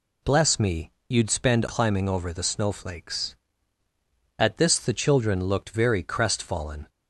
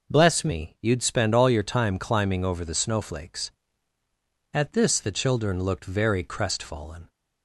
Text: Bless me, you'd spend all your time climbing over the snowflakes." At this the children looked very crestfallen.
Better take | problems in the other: second | skips "all your time"; at 1.6 s

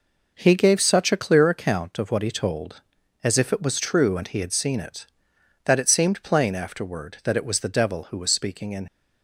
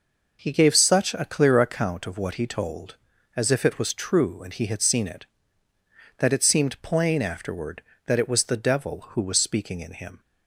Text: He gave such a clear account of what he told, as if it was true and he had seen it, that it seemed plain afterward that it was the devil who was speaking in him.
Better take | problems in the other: second | stops before "him"; at 8.8 s

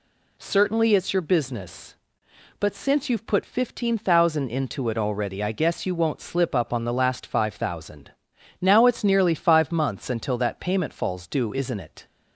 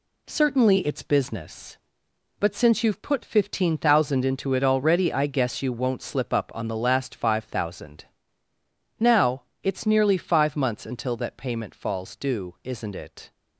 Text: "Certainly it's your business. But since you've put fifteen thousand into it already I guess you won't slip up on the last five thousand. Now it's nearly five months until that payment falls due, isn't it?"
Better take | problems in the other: first | skips "your"; at 1.0 s // pauses between "Now" and "it's"; slight; at 9.4 s; 0.22 s long

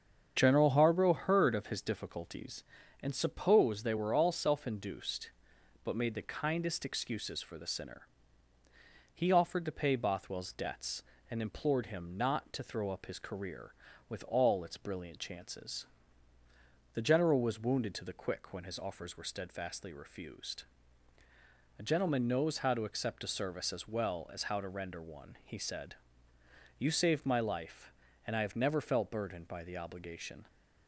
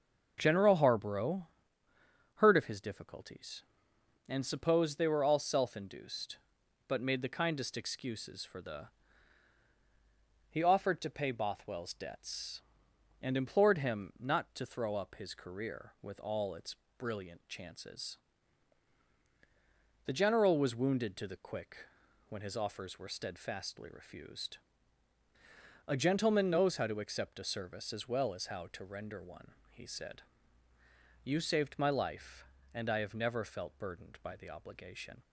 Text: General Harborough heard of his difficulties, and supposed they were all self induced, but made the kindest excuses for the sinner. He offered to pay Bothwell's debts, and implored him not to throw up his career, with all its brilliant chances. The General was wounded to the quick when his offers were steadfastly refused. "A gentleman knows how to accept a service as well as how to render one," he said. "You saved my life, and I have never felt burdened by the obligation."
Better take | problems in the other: first | starts louder than the rest; noticeable; until 1.3 s; 6 dB; strong in the first // pauses between "Harborough" and "heard"; noticeable; at 1.4 s; 0.86 s long // skips "sinner"; at 9.6 s // pauses between "its" and "brilliant"; slight; at 16.7 s; 0.22 s long // pauses between "quick" and "when"; at 21.8 s; 0.44 s long

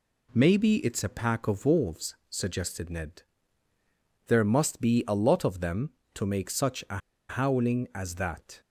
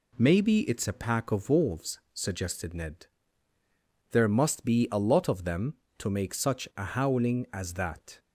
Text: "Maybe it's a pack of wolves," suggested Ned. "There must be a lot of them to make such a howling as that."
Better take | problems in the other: second | pauses between "a" and "howling"; slight; at 6.9 s; 0.31 s long

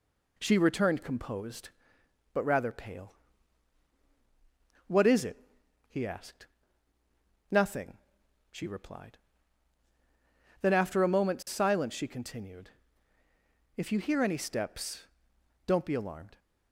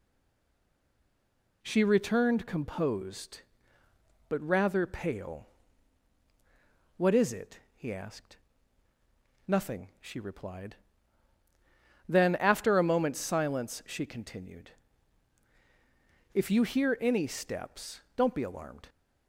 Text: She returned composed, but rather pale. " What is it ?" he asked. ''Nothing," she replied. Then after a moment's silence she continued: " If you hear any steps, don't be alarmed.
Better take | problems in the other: first | stays silent before the first word; noticeable; until 1.6 s; 1.6 s long

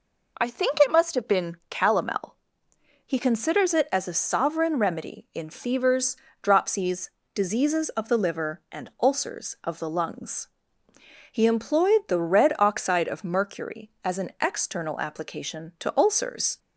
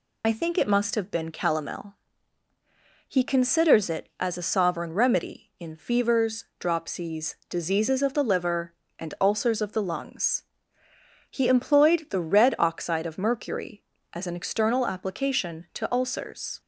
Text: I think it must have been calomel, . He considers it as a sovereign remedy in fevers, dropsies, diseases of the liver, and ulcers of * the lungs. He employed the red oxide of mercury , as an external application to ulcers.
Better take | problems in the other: first | loses the start of "I"; at 0.2 s; 40 ms

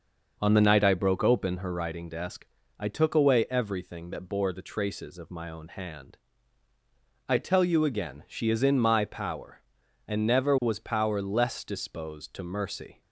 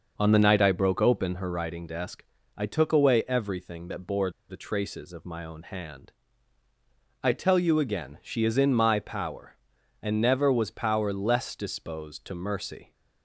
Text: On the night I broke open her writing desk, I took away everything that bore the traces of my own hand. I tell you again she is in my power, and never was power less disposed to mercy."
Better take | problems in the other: first | pauses between "bore" and "the"; slight; at 4.2 s; 0.19 s long

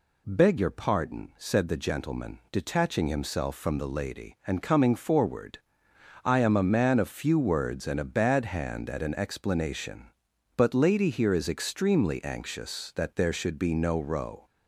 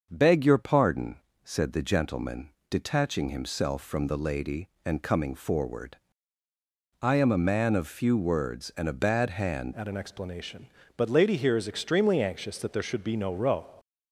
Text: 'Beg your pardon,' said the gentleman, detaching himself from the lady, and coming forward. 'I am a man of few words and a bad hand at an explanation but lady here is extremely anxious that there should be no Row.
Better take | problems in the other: first | starts louder than the rest; until 1.1 s; 6.5 dB // changes voice at "at"; from 9.7 s on; 3.9 s long

